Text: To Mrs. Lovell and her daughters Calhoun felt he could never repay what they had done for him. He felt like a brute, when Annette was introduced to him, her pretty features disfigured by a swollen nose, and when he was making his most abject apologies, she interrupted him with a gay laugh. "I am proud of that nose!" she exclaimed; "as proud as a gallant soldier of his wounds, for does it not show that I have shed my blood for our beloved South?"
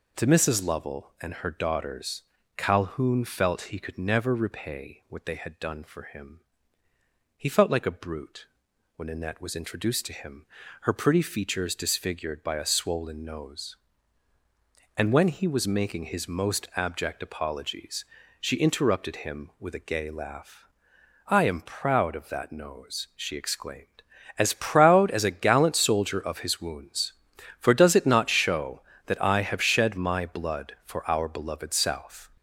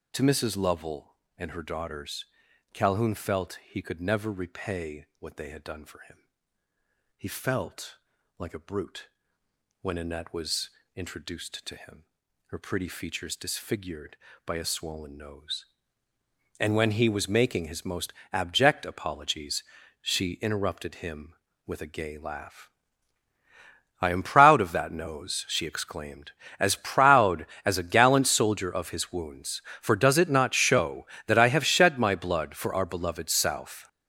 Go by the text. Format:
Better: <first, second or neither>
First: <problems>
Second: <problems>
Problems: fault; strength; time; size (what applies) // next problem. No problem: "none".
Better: first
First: pauses between "daughters" and "Calhoun"; slight; at 2.2 s; 0.34 s long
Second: gets louder; strong; throughout; 10 dB // pauses between "daughters" and "Calhoun"; noticeable; at 2.2 s; 0.48 s long // pauses between "felt" and "like"; at 7.9 s; 0.42 s long // pauses between "was" and "introduced"; slight; at 10.6 s; 0.26 s long // pauses between "most" and "abject"; slight; at 18.1 s; 0.20 s long